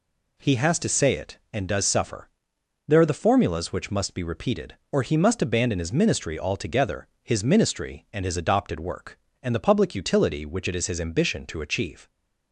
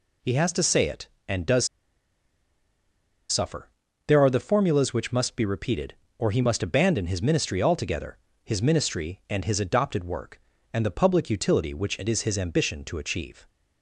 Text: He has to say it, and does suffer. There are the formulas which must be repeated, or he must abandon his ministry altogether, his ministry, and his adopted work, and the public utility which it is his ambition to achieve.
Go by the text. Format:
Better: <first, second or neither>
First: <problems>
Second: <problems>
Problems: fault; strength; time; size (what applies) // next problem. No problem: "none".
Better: first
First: none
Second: pauses between "does" and "suffer"; strong; at 1.6 s; 1.6 s long